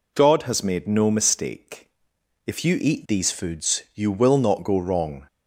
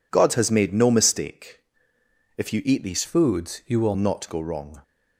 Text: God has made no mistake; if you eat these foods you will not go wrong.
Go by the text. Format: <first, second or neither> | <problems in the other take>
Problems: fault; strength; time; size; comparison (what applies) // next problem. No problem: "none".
first | changes voice from "foods" to "will"; from 3.0 to 3.9 s; 0.9 s long